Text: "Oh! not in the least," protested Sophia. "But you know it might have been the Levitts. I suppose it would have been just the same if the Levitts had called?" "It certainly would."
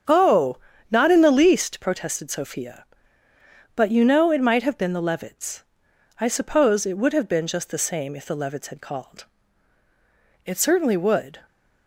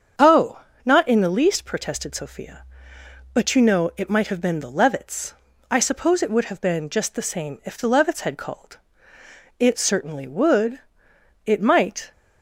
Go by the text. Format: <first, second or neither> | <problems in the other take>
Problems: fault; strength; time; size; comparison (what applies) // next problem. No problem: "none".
first | starts louder than the rest; strong; until 1.4 s; 7.5 dB; strong in the first // goes on to say "It might"; noticeable; from 11.4 s on; 0.66 s long